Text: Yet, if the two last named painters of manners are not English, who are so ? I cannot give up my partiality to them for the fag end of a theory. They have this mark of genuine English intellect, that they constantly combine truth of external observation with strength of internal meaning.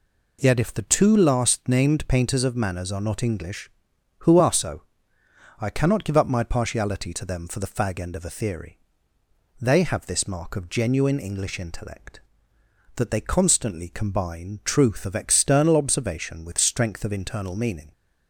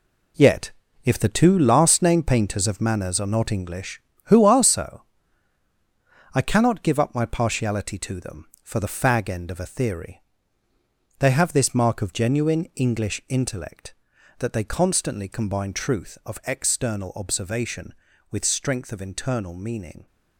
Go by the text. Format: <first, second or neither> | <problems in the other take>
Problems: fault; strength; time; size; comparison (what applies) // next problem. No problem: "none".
first | gets quieter; strong; throughout; 8.5 dB